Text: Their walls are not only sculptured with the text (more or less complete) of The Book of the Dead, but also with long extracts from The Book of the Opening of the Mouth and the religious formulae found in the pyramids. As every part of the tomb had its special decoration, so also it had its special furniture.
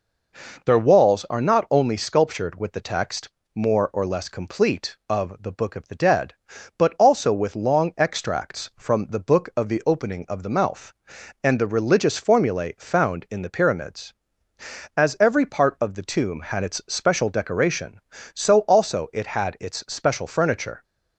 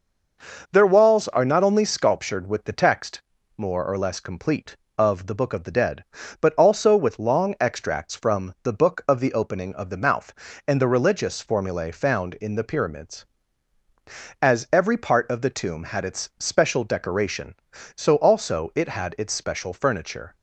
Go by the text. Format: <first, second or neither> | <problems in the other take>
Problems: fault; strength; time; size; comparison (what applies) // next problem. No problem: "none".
neither | none